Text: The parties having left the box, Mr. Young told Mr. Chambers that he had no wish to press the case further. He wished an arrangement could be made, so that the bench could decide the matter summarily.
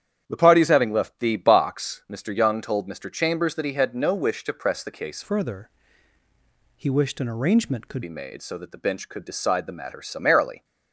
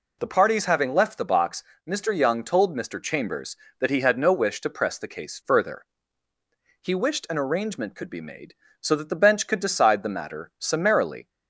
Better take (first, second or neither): second